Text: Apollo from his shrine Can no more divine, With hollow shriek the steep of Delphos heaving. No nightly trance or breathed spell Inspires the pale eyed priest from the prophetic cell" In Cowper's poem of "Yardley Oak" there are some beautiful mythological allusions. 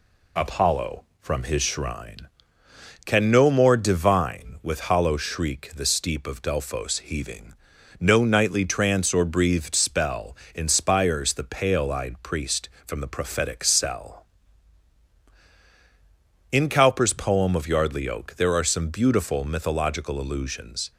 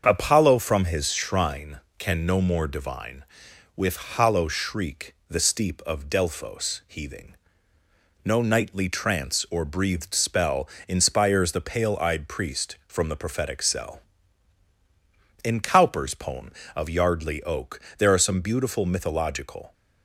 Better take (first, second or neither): first